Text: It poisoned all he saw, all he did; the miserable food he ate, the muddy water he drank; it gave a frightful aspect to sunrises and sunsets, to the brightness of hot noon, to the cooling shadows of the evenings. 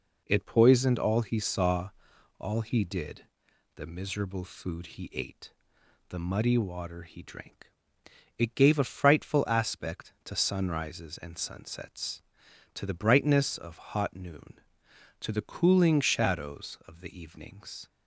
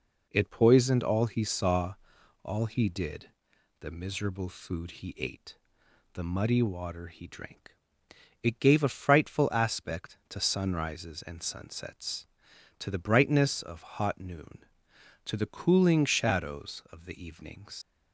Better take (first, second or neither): first